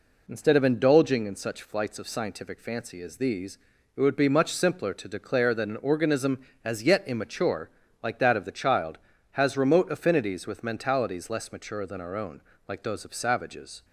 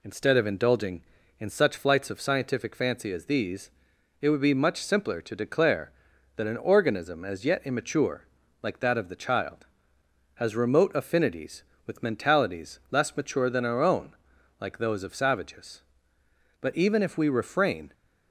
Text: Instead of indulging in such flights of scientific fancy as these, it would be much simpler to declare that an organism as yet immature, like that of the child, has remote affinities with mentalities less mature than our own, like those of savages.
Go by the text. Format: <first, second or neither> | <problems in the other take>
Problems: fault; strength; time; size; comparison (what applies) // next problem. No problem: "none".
first | goes on to say "But even if we refrain"; from 16.6 s on; 1.3 s long